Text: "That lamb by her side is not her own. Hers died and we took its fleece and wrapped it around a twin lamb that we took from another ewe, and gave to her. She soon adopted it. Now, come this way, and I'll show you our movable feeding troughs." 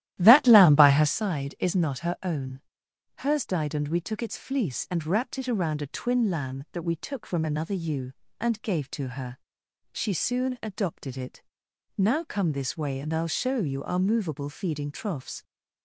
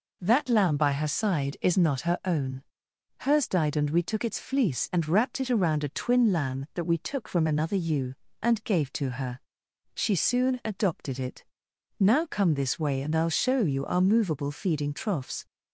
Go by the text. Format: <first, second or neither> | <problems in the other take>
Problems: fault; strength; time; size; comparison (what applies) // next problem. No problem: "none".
second | starts louder than the rest; strong; until 1.2 s; 13.5 dB